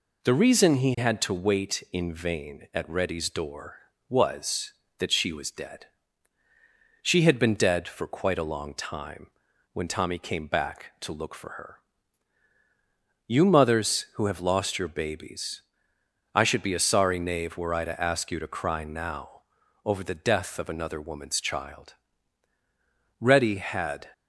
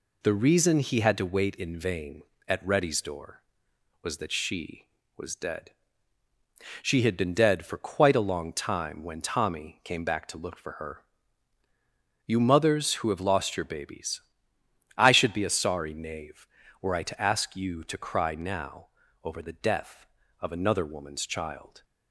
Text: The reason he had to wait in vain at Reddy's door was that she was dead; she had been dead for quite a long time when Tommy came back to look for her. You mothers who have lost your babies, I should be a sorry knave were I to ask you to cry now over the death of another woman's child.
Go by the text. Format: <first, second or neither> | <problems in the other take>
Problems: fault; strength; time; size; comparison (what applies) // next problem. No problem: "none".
second | pauses between "time" and "when"; at 9.3 s; 0.42 s long // pauses between "now" and "over"; at 19.4 s; 0.42 s long; slight in the second // goes on to say "Reddy had"; noticeable; from 23.1 s on; 0.88 s long